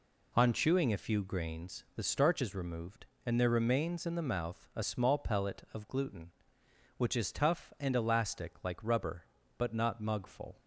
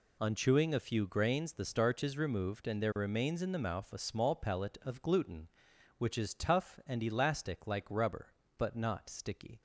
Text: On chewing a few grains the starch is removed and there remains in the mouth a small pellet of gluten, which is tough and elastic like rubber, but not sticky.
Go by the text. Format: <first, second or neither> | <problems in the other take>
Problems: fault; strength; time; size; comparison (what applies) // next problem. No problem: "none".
second | says "mugful" for "sticky"; at 10.0 s